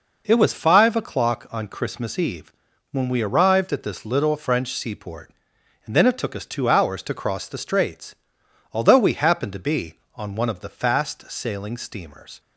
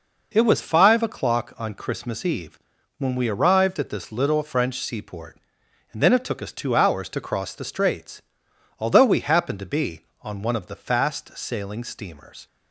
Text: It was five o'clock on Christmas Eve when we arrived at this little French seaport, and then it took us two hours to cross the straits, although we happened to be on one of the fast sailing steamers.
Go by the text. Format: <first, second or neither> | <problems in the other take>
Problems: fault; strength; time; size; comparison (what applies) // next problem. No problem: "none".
neither | pauses between "Eve" and "when"; the same in both